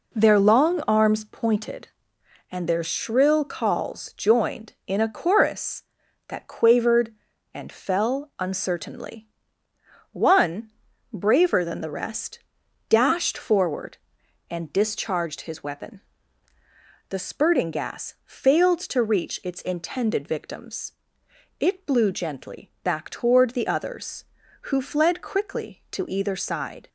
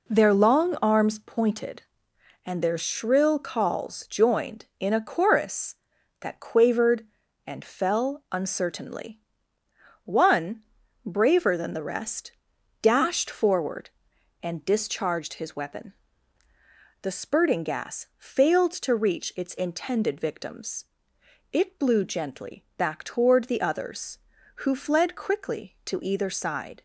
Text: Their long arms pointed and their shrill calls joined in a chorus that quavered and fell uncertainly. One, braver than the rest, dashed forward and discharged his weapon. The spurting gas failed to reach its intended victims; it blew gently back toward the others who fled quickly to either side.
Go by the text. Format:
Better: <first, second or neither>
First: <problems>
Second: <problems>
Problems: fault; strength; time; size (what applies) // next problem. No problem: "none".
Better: neither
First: none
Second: none